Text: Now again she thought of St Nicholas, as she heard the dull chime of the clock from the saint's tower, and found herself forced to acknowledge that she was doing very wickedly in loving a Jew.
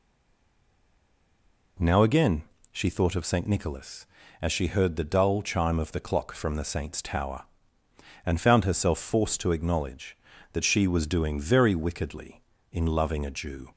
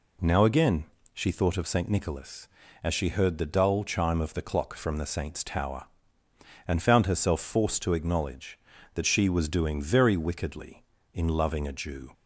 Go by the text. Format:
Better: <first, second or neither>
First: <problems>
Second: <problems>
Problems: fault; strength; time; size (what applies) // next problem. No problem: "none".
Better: second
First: stays silent before the first word; noticeable; until 1.7 s; 1.7 s long // pauses between "again" and "she"; slight; at 2.4 s; 0.30 s long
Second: pauses between "again" and "she"; slight; at 0.8 s; 0.30 s long